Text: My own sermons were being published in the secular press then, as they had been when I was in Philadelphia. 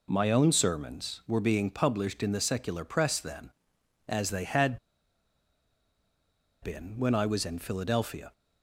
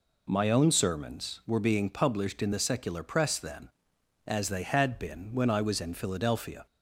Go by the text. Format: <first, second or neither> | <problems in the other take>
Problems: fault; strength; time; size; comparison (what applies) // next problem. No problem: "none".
second | pauses between "had" and "been"; strong; at 4.7 s; 1.8 s long